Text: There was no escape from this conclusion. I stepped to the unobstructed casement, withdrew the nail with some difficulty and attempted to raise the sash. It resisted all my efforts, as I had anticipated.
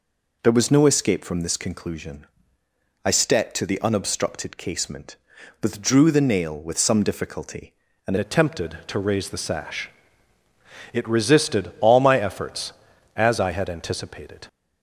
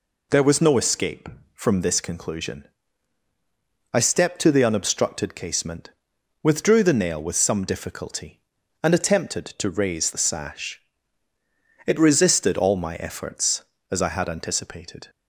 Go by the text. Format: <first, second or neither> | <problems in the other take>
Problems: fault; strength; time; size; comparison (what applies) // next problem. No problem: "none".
second | changes voice at "attempted"; from 8.1 s on; 6.3 s long